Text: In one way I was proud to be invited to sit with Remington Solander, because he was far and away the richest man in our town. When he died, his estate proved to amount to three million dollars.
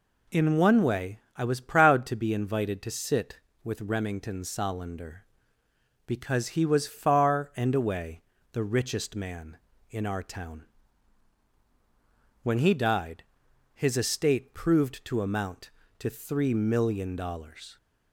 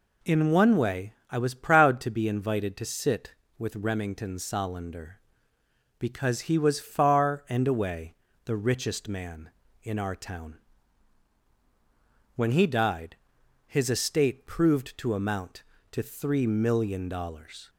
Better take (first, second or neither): neither